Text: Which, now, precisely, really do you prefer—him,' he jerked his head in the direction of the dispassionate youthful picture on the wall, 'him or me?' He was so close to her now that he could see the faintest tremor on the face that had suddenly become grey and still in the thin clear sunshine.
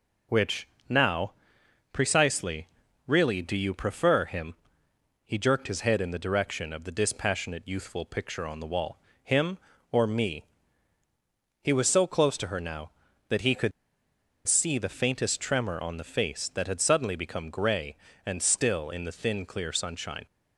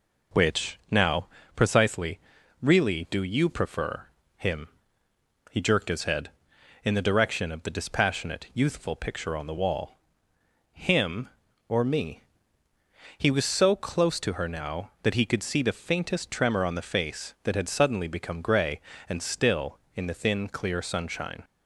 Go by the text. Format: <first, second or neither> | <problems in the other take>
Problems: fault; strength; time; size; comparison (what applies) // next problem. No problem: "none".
second | pauses between "could" and "see"; noticeable; at 13.7 s; 0.76 s long